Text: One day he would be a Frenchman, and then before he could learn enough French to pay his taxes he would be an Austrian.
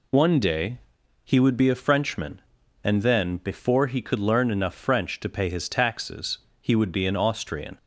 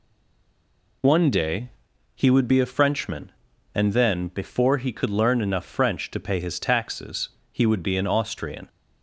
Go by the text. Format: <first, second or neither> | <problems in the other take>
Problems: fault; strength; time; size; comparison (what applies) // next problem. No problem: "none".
first | stays silent before the first word; until 1.0 s; 1.0 s long // pauses between "day" and "he"; noticeable; at 1.6 s; 0.46 s long; noticeable in the first // pauses between "taxes" and "he"; slight; at 7.2 s; 0.22 s long; slight in the first